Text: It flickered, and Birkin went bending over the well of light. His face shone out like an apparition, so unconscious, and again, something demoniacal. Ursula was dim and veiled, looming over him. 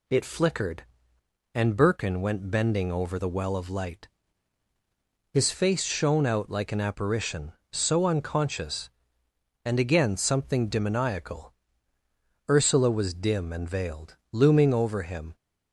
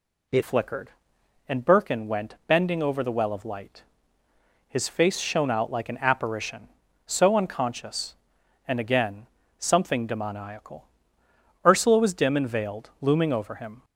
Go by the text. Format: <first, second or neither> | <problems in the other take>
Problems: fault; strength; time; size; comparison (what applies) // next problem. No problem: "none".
first | changes voice at "flickered"; from 0.4 s on; 13.4 s long